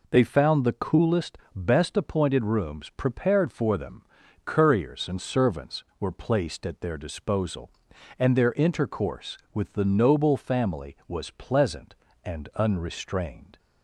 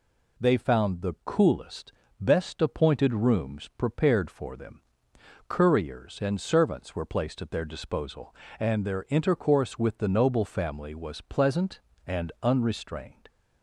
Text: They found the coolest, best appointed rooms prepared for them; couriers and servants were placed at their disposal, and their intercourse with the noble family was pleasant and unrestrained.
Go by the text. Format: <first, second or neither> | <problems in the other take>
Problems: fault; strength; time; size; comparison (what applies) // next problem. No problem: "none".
neither | none